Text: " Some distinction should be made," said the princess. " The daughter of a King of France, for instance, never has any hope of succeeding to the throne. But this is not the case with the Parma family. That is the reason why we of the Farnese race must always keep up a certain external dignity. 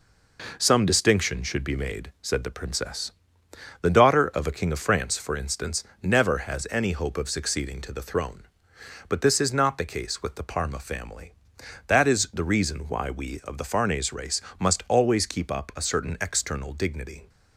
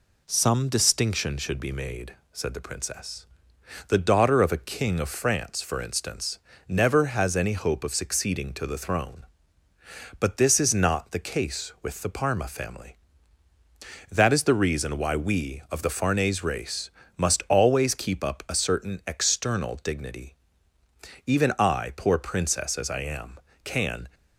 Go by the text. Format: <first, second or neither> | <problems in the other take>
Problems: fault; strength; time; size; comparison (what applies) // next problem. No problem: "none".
first | pauses between "race" and "must"; slight; at 16.8 s; 0.28 s long; slight in the first // goes on to say "Even I poor princess as I am can"; strong; from 21.2 s on; 2.8 s long